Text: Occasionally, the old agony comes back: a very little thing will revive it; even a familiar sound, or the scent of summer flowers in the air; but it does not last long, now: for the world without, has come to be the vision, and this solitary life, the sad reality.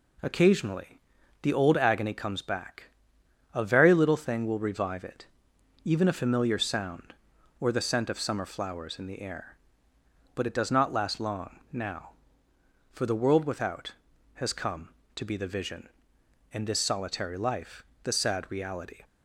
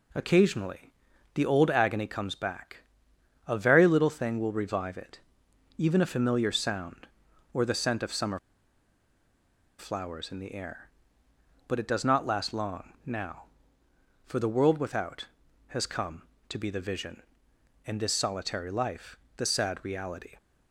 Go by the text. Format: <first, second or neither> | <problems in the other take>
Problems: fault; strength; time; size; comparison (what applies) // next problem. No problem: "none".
first | pauses between "summer" and "flowers"; strong; at 8.3 s; 1.4 s long